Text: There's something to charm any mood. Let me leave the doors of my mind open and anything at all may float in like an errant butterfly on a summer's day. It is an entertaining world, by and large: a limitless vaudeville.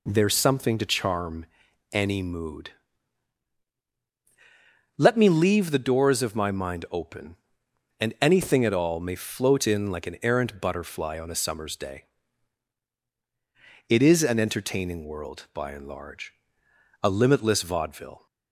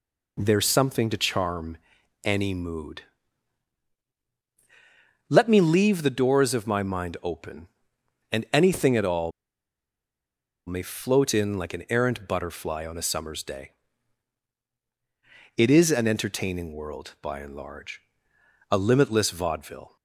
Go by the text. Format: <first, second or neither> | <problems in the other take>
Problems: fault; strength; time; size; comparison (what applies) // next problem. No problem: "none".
first | pauses between "charm" and "any"; at 1.7 s; 0.44 s long; also in the first // pauses between "all" and "may"; strong; at 9.3 s; 1.3 s long